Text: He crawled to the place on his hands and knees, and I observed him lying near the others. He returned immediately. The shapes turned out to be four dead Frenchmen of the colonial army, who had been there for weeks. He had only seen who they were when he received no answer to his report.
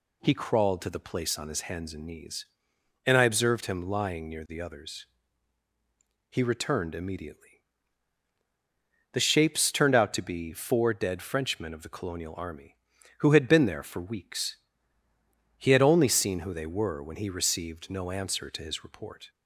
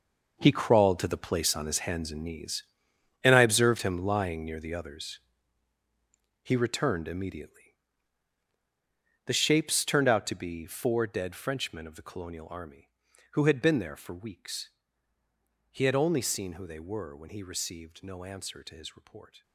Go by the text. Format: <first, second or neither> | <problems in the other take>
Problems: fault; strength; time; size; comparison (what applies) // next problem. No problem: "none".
first | gets quieter; strong; throughout; 13.5 dB